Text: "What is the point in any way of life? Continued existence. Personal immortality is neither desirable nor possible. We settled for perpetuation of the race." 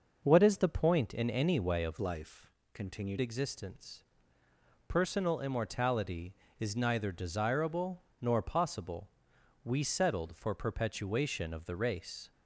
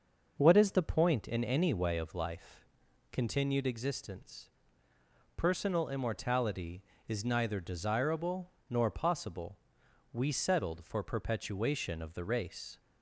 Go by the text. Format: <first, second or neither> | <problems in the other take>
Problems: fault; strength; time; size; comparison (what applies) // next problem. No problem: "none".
second | changes voice from "life" to "Continued"; from 2.0 to 3.1 s; 1.1 s long // pauses between "desirable" and "nor"; slight; at 8.0 s; 0.20 s long; slight in the second